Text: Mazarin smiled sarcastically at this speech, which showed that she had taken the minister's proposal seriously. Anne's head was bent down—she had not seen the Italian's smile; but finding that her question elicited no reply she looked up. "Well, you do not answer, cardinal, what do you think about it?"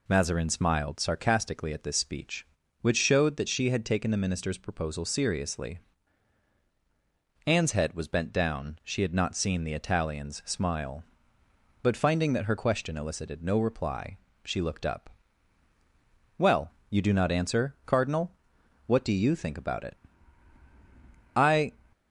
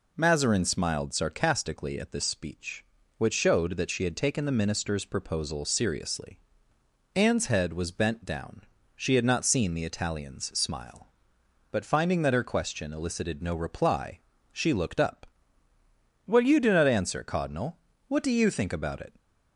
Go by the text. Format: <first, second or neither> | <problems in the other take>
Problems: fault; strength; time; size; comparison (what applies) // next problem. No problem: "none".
second | pauses between "reply" and "she"; slight; at 14.1 s; 0.26 s long; slight in the second // goes on to say "I"; slight; from 21.3 s on; 0.38 s long